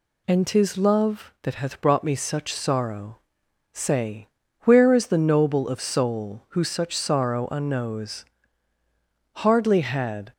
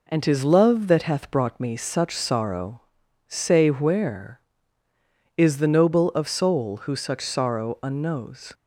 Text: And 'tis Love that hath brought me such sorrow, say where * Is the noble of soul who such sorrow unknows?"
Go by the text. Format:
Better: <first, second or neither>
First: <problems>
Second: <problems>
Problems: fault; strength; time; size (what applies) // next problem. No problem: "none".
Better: second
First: pauses between "say" and "where"; slight; at 4.2 s; 0.34 s long // goes on to say "Hardly had"; noticeable; from 9.3 s on; 0.98 s long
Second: none